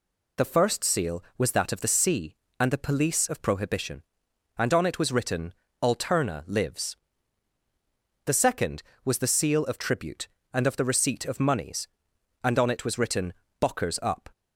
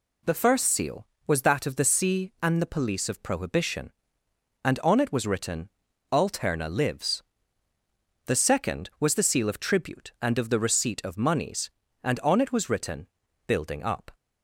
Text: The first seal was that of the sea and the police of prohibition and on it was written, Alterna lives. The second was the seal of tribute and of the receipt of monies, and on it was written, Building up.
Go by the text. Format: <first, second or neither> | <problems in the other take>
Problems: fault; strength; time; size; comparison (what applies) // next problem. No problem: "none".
second | says "Bockers" for "Building"; at 13.5 s